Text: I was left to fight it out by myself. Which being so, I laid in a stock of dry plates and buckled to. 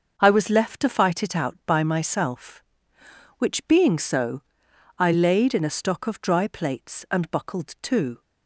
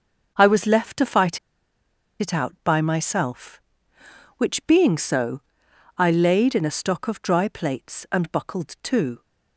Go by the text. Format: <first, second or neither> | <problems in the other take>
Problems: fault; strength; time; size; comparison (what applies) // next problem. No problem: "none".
first | starts louder than the rest; noticeable; until 1.3 s; 6 dB; noticeable in the first // pauses between "fight" and "it"; noticeable; at 1.3 s; 0.82 s long